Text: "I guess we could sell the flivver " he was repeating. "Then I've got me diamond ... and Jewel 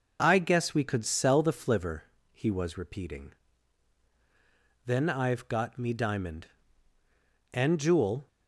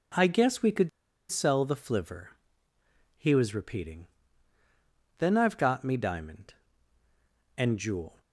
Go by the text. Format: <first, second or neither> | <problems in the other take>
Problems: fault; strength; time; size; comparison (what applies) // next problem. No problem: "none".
first | pauses between "could" and "sell"; at 0.8 s; 0.40 s long